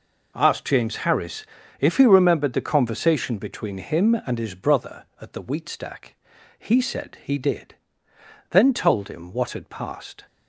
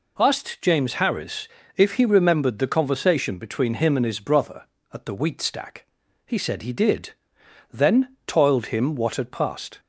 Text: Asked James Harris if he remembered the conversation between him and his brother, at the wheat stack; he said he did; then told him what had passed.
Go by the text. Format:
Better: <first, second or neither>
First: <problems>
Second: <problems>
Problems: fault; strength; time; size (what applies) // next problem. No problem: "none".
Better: first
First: pauses between "Harris" and "if"; slight; at 1.4 s; 0.36 s long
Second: pauses between "Harris" and "if"; slight; at 1.4 s; 0.30 s long // says "toiled" for "told"; at 8.2 s